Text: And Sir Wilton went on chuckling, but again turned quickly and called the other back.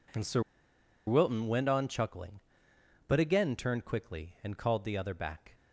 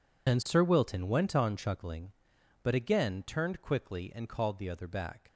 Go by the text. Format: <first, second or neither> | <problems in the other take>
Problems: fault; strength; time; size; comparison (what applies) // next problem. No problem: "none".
second | pauses between "Sir" and "Wilton"; noticeable; at 0.4 s; 0.66 s long